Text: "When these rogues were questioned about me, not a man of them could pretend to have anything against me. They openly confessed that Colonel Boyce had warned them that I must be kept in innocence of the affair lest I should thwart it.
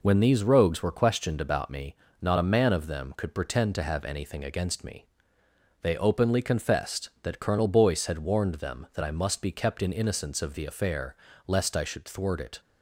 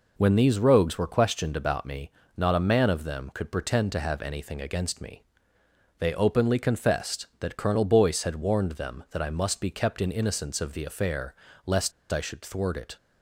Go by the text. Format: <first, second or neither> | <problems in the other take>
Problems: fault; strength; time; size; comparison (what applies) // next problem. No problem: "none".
first | pauses between "affair" and "lest"; slight; at 11.3 s; 0.30 s long; slight in the first // pauses between "lest" and "I"; slight; at 11.9 s; 0.20 s long